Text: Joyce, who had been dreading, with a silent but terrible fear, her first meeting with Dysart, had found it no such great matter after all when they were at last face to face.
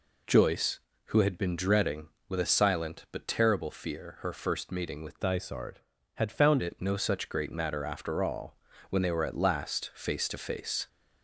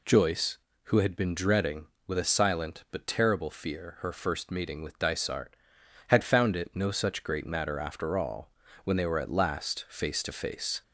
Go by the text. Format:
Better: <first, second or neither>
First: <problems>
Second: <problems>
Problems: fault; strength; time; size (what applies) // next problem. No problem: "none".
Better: second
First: changes voice from "Dysart" to "found"; from 5.1 to 6.6 s; 1.5 s long // pauses between "all" and "when"; slight; at 8.5 s; 0.34 s long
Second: pauses between "all" and "when"; slight; at 8.5 s; 0.34 s long